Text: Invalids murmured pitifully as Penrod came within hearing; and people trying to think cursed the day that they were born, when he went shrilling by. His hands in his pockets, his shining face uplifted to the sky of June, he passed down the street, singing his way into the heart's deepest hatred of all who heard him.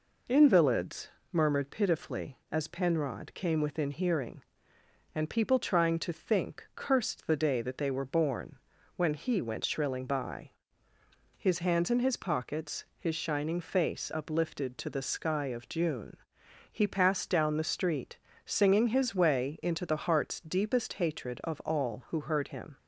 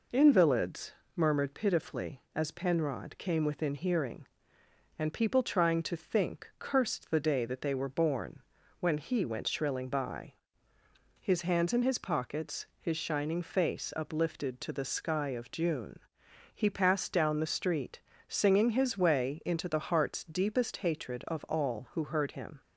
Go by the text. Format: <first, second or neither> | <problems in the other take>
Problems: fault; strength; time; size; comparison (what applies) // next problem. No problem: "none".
neither | pauses between "Invalids" and "murmured"; slight; the same in both